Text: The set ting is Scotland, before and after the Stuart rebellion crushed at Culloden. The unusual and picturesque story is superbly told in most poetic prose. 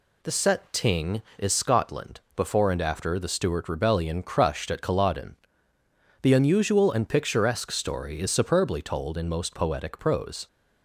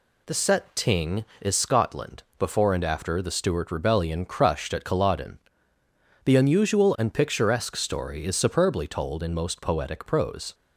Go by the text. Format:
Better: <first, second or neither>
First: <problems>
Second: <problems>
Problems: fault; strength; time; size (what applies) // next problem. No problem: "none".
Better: neither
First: none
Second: none